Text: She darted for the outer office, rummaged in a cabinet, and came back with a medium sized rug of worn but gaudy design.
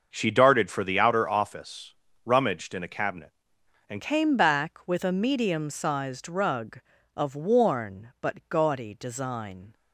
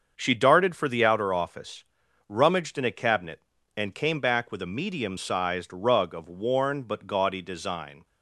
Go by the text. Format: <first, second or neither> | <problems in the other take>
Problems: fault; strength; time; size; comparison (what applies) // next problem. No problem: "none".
second | starts louder than the rest; until 1.1 s; 6.5 dB; also in the second // changes voice at "came"; from 3.9 s on; 5.8 s long